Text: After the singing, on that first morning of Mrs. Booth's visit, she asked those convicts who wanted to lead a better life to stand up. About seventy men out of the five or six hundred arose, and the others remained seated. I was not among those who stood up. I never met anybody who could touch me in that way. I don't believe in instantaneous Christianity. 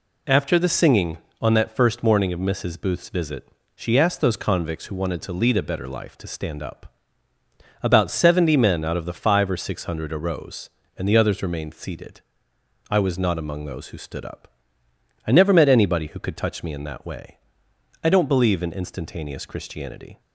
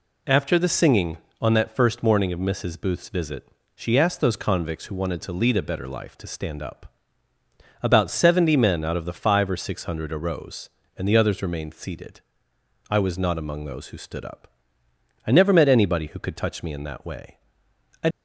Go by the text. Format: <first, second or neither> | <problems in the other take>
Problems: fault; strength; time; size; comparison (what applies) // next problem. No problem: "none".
first | stops before "don't believe in instantaneous Christianity"; at 18.1 s